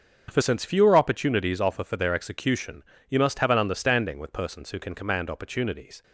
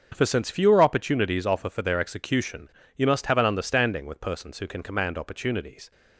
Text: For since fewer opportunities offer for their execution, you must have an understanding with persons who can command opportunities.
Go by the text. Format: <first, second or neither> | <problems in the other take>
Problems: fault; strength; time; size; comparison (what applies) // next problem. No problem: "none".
neither | starts louder than the rest; the same in both